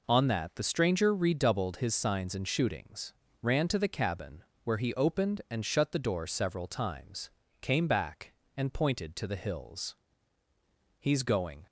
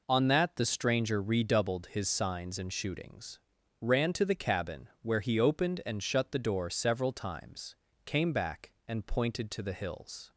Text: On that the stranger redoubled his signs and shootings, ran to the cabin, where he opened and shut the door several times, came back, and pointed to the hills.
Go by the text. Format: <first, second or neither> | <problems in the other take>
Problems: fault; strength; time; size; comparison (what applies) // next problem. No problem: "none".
second | goes on to say "He's going"; noticeable; from 10.9 s on; 0.68 s long